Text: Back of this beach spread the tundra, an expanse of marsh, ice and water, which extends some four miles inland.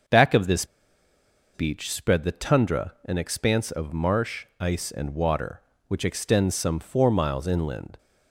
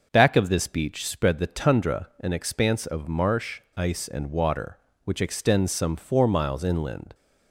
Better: second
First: starts louder than the rest; noticeable; until 1.9 s; 6 dB // pauses between "this" and "beach"; noticeable; at 0.6 s; 0.89 s long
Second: starts louder than the rest; noticeable; until 1.1 s; 6 dB

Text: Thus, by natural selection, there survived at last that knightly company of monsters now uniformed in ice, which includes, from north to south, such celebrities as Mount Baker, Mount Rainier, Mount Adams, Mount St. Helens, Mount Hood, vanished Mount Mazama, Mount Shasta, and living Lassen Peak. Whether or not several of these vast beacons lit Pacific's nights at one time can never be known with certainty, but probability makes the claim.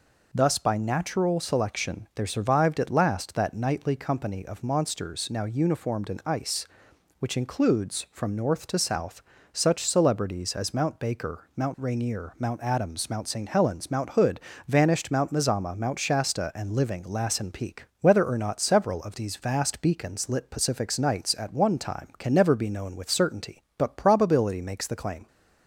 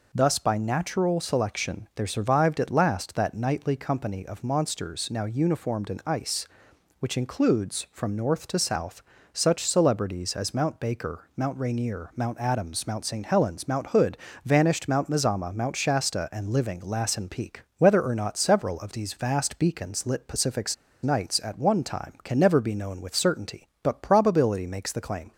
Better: first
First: none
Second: pauses between "Pacific's" and "nights"; slight; at 20.7 s; 0.29 s long

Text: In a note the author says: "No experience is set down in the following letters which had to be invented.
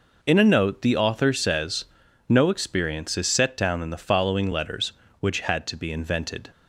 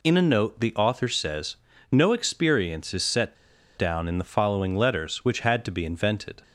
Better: first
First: none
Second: pauses between "set" and "down"; at 3.3 s; 0.42 s long

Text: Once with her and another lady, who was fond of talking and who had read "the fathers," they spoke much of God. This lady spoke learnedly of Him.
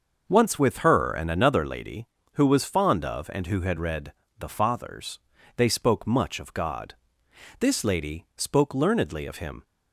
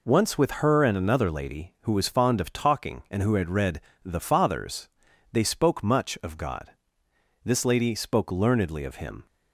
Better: second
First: starts louder than the rest; noticeable; until 1.2 s; 6 dB // skips "talking"; at 3.3 s // pauses between "read" and "the"; slight; at 4.1 s; 0.28 s long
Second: pauses between "read" and "the"; slight; at 3.7 s; 0.24 s long

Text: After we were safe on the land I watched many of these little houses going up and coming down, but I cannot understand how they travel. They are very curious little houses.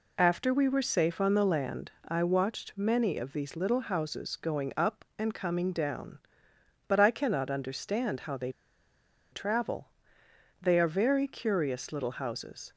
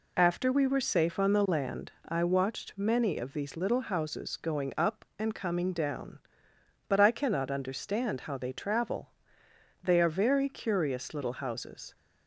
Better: second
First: pauses between "land" and "I"; slight; at 1.9 s; 0.16 s long // pauses between "they" and "travel"; noticeable; at 8.5 s; 0.79 s long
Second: pauses between "land" and "I"; slight; at 1.9 s; 0.16 s long

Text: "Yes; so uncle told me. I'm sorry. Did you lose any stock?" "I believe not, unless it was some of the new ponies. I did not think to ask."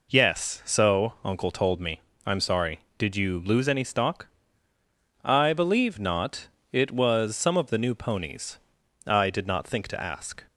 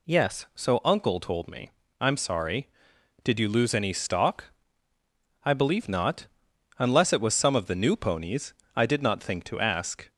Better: second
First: skips "unless"; at 6.5 s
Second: none

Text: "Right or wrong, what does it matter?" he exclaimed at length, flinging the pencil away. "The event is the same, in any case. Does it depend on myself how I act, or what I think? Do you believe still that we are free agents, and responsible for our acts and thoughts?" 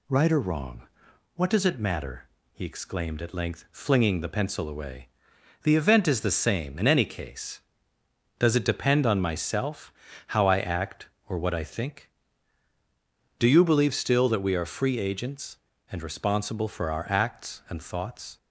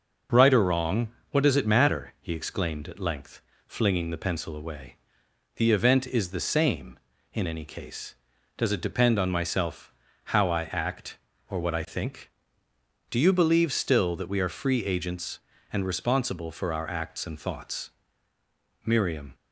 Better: first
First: pauses between "myself" and "how"; slight; at 9.9 s; 0.36 s long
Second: pauses between "myself" and "how"; slight; at 9.9 s; 0.32 s long // goes on to say "Miriam"; slight; from 18.8 s on; 0.48 s long

